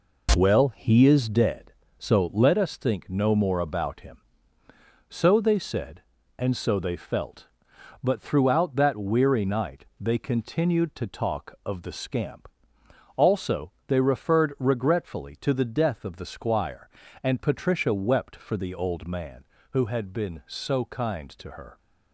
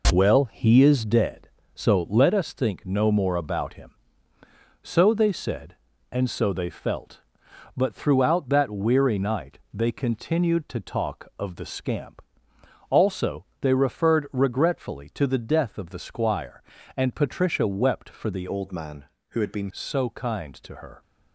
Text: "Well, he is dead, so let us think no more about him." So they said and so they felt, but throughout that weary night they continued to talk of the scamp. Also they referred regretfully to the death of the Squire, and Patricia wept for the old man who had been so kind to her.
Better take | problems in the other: first | pauses between "night" and "they"; slight; at 9.5 s; 0.16 s long; slight in the first // pauses between "Also" and "they"; slight; at 13.4 s; 0.16 s long; slight in the first // changes voice from "old" to "been"; from 18.4 to 19.7 s; 1.3 s long

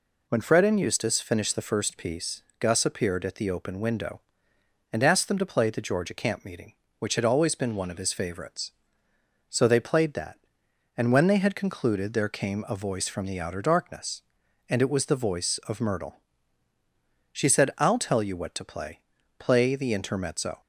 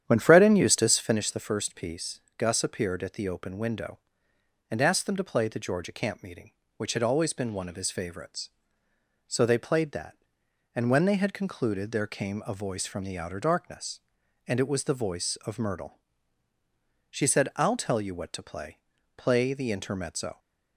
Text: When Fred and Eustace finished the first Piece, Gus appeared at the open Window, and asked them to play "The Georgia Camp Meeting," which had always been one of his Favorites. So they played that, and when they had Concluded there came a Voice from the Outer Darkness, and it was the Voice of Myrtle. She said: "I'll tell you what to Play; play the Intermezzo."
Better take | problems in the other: first | starts louder than the rest; strong; until 1.2 s; 9.5 dB

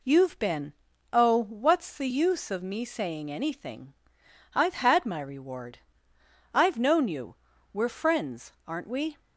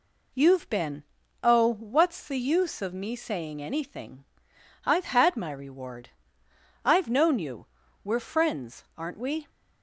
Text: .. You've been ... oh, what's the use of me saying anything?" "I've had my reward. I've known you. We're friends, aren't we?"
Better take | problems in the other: neither | none

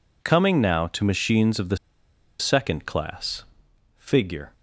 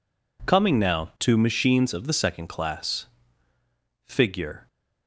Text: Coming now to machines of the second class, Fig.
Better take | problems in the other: second | pauses between "the" and "second"; noticeable; at 1.7 s; 0.62 s long

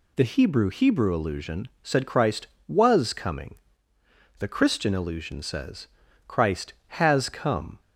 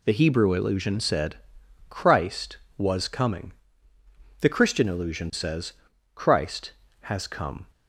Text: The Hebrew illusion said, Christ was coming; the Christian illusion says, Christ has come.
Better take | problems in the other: second | says "Hebrew" twice; at 0.7 s // pauses between "illusion" and "said"; slight; at 1.6 s; 0.16 s long

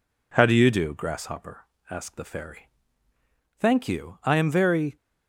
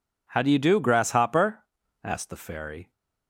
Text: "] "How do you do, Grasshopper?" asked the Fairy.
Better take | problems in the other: second | goes on to say "Thank you I am very"; from 3.5 s on; 1.3 s long

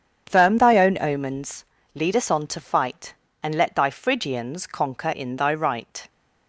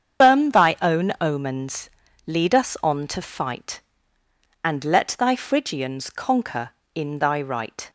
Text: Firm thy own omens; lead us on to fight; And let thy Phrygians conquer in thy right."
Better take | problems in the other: first | loses the start of "Firm"; at 0.2 s; 210 ms // starts louder than the rest; strong; until 1.3 s; 7.5 dB; strong in the first

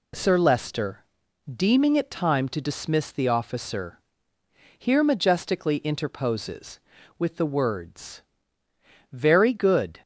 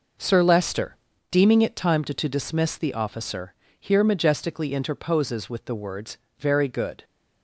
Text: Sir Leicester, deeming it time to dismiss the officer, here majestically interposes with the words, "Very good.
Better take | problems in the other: first | says "to" twice; at 2.1 s

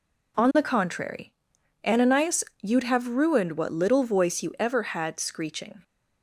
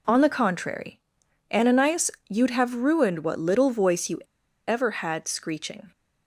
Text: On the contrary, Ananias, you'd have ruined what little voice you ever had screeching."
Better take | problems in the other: first | pauses between "you" and "ever"; at 4.2 s; 0.45 s long

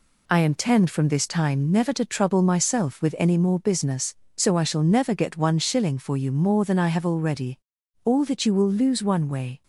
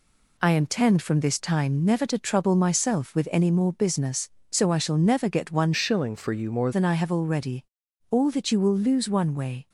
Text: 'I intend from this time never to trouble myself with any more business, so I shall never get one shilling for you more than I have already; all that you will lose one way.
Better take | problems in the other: first | changes voice from "shilling" to "more"; from 5.7 to 6.7 s; 1.0 s long

